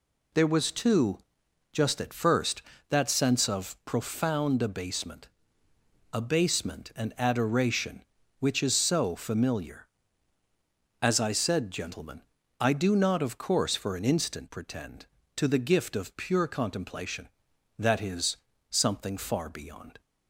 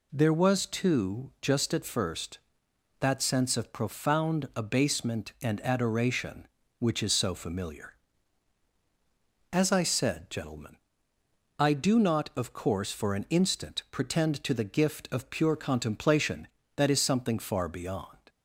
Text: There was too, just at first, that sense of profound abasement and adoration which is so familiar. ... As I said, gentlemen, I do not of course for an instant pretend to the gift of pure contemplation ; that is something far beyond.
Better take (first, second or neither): second